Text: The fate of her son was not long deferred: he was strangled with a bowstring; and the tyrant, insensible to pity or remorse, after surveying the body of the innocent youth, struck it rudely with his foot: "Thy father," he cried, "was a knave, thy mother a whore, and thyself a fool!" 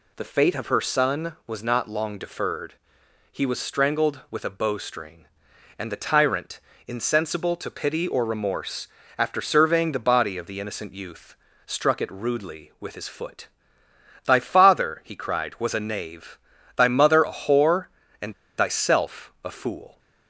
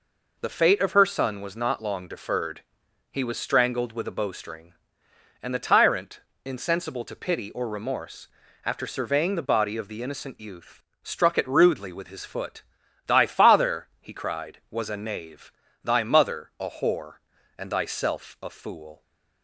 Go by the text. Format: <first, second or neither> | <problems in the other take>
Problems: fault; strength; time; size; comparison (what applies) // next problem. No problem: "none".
second | pauses between "and" and "thyself"; slight; at 18.3 s; 0.24 s long